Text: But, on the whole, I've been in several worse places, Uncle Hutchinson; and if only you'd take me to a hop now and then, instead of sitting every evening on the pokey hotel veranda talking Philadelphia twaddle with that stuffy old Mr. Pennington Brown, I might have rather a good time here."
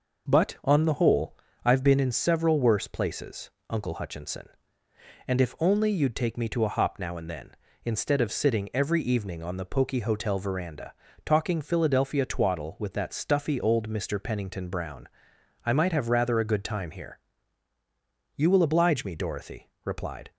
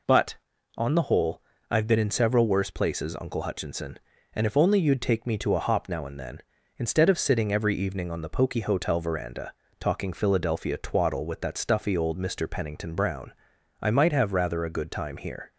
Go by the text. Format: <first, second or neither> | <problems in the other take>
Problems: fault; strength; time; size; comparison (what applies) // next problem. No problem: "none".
second | pauses between "veranda" and "talking"; slight; at 10.9 s; 0.32 s long; slight in the second // goes on to say "You will oblige me Dorothy replied"; strong; from 18.3 s on; 1.9 s long